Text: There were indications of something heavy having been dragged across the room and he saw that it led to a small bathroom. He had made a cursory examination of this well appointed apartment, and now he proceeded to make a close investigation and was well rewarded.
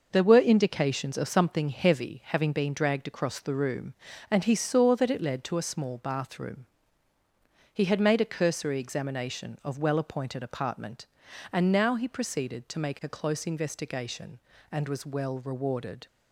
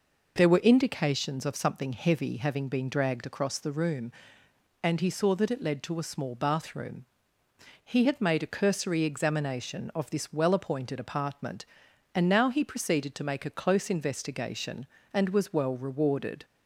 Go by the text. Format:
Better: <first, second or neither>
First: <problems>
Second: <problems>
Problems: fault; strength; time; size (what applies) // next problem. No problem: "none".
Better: second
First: skips "this"; at 9.7 s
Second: none